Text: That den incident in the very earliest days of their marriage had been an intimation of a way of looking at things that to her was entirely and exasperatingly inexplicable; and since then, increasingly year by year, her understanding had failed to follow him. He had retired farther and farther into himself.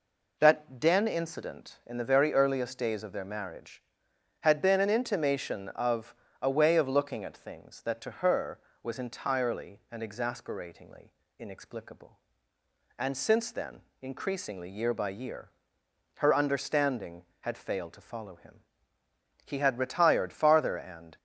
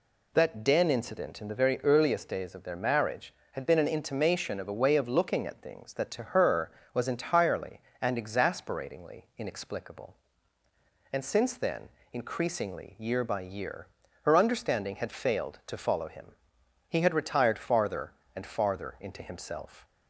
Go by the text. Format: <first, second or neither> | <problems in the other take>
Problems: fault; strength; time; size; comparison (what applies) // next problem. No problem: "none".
second | pauses between "of" and "a"; slight; at 6.1 s; 0.28 s long // pauses between "exasperatingly" and "inexplicable"; slight; at 11.1 s; 0.28 s long // stops before "farther into himself"; at 21.1 s